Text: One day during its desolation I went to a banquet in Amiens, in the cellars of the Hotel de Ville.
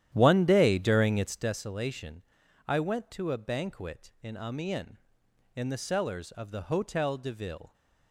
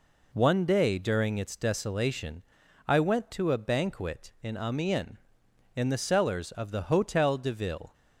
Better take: second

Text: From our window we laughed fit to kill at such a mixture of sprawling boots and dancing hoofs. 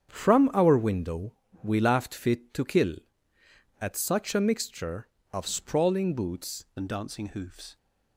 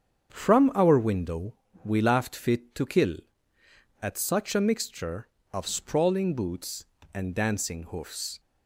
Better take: second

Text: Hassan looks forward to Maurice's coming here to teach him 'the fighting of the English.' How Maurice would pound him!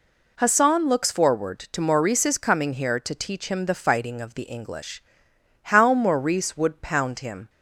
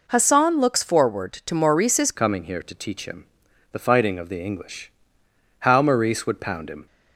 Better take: first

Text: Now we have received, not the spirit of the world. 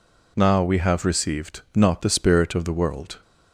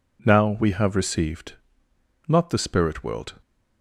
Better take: first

